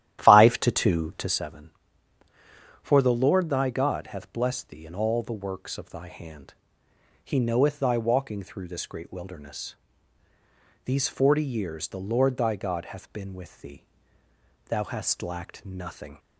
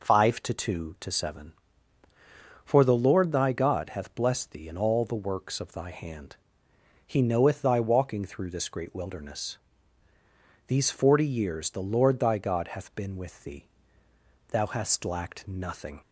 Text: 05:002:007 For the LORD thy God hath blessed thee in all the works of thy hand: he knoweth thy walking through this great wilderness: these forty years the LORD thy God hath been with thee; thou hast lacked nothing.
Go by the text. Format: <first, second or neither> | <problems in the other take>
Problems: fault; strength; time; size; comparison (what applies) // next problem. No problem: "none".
second | starts louder than the rest; strong; until 1.4 s; 12.5 dB